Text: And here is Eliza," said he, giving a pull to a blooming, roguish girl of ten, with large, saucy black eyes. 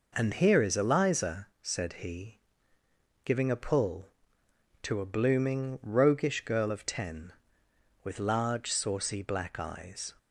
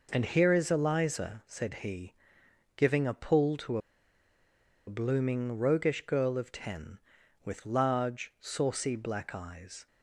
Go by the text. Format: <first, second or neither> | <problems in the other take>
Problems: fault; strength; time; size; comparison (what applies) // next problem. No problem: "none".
first | pauses between "to" and "a"; at 3.7 s; 1.0 s long